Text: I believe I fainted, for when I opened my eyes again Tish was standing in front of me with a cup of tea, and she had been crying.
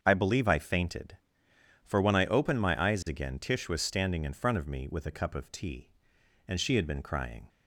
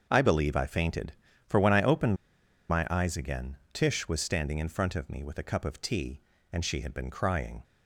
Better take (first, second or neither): first